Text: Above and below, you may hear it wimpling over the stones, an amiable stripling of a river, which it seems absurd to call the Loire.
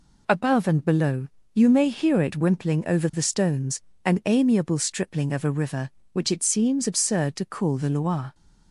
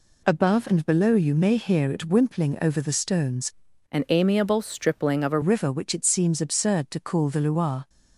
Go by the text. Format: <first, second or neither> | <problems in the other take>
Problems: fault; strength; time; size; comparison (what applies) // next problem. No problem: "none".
first | changes voice from "an" to "a"; from 3.8 to 5.3 s; 1.5 s long